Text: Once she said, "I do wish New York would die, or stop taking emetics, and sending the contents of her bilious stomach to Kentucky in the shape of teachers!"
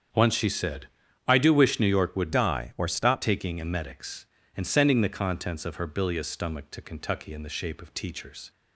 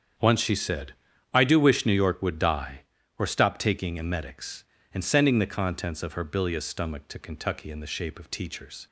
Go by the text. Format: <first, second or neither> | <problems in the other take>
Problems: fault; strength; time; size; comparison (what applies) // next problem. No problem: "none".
second | starts louder than the rest; strong; until 1.5 s; 7.5 dB; strong in the second // changes voice from "die" to "stop"; from 2.3 to 3.2 s; 0.9 s long